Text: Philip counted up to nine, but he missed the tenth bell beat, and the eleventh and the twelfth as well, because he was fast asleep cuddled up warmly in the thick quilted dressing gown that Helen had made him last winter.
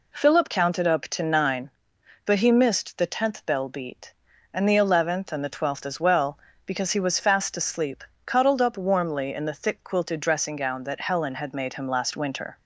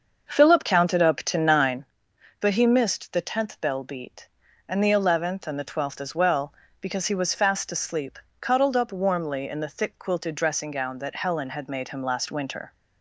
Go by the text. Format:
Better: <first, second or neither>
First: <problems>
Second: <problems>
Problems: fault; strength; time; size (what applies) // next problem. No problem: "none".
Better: first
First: pauses between "asleep" and "cuddled"; slight; at 8.0 s; 0.22 s long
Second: starts louder than the rest; until 1.9 s; 6.5 dB // pauses between "asleep" and "cuddled"; slight; at 8.1 s; 0.22 s long